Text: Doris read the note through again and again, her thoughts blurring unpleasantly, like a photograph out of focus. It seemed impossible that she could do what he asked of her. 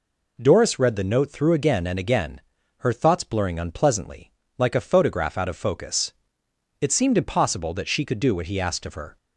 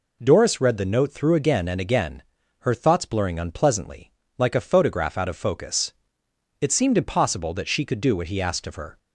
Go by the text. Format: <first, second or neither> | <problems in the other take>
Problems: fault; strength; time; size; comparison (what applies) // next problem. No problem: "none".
neither | none